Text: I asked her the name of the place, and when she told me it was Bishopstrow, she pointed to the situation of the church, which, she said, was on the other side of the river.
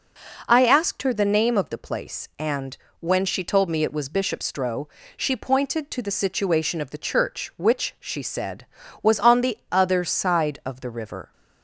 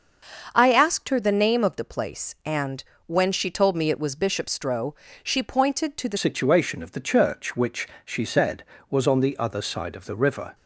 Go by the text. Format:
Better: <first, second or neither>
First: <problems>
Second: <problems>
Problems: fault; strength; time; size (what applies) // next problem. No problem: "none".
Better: first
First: pauses between "and" and "when"; slight; at 2.7 s; 0.26 s long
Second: starts louder than the rest; until 1.5 s; 6.5 dB // pauses between "and" and "when"; slight; at 2.8 s; 0.26 s long // changes voice at "situation"; from 6.1 s on; 4.4 s long